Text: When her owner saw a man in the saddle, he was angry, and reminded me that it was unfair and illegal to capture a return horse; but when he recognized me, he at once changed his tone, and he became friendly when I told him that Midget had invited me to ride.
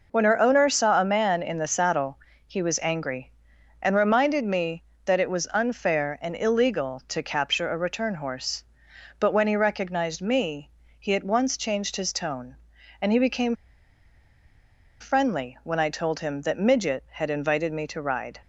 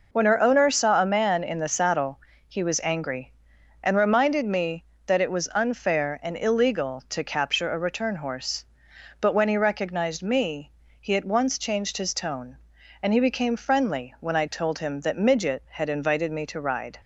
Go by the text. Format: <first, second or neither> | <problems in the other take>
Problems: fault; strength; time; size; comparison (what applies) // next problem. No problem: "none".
second | pauses between "became" and "friendly"; strong; at 13.5 s; 1.4 s long